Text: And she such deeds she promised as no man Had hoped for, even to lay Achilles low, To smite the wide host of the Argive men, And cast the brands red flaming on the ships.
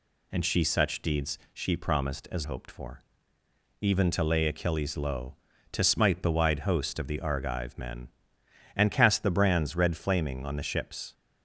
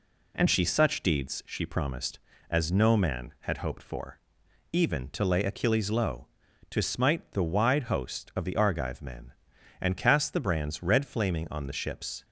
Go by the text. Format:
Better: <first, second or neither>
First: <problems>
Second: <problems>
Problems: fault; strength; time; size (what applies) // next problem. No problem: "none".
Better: second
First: skips "no man Had"; at 2.4 s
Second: none